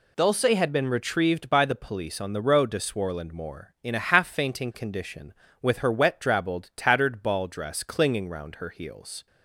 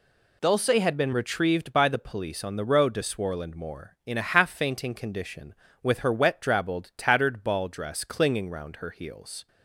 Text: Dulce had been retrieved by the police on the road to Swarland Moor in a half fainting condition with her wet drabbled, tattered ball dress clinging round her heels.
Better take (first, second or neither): neither